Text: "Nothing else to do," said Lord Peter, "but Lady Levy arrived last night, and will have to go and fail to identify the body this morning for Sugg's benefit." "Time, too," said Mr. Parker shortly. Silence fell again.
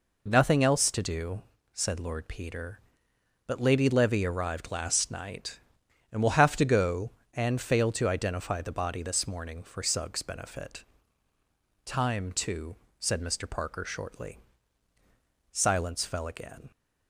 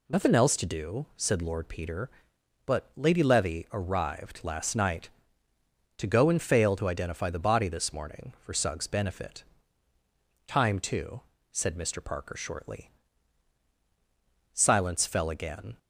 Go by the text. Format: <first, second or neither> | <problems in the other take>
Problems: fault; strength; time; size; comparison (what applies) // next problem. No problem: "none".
first | skips "and will have"; at 5.5 s